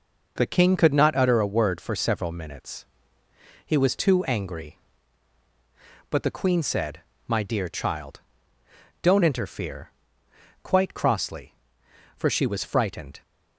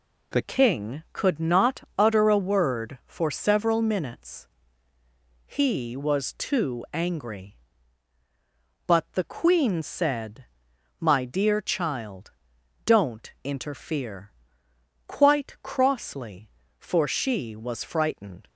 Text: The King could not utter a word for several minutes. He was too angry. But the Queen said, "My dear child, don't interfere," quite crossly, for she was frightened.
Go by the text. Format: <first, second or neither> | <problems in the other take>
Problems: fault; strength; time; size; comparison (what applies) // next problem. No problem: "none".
first | changes voice at "King"; from 0.4 s on; 18.0 s long